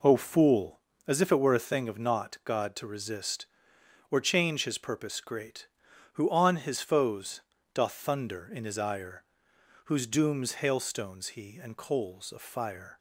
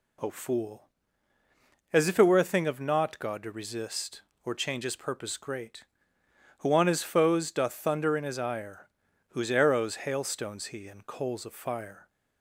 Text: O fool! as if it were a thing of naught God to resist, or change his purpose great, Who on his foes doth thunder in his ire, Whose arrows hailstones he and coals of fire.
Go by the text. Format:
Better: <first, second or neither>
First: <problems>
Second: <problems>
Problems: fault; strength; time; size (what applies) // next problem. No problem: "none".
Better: second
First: pauses between "foes" and "doth"; slight; at 7.4 s; 0.34 s long // says "dooms" for "arrows"; at 10.0 s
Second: none